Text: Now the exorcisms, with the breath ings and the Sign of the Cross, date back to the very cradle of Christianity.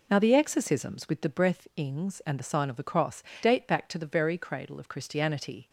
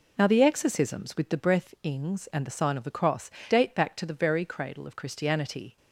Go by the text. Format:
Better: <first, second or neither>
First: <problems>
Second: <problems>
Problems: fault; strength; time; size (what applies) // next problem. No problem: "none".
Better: neither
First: none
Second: none